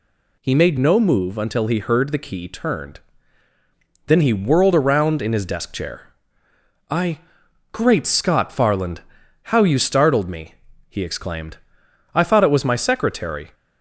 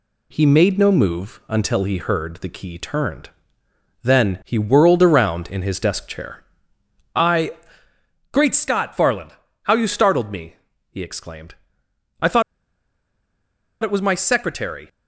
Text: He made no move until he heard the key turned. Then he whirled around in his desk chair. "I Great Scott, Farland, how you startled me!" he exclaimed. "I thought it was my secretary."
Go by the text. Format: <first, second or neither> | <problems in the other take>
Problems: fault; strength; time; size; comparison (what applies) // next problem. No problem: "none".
first | pauses between "I" and "Great"; noticeable; at 7.5 s; 0.80 s long; noticeable in the first // pauses between "thought" and "it"; strong; at 12.4 s; 1.4 s long